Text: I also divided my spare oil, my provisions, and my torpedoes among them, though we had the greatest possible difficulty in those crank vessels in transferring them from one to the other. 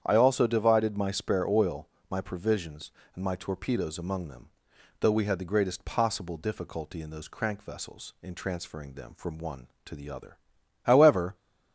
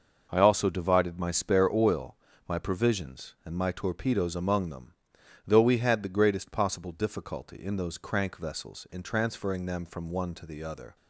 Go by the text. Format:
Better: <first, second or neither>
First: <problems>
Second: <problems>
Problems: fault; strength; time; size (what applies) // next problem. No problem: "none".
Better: second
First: starts louder than the rest; strong; until 1.0 s; 9 dB // goes on to say "However"; from 10.8 s on; 0.52 s long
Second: none